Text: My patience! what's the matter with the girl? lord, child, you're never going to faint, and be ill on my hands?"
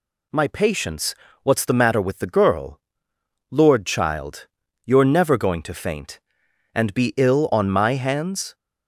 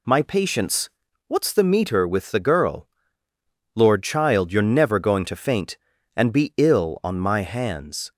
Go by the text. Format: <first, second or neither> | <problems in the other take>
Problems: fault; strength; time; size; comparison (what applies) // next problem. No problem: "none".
first | says "meter" for "matter"; at 1.6 s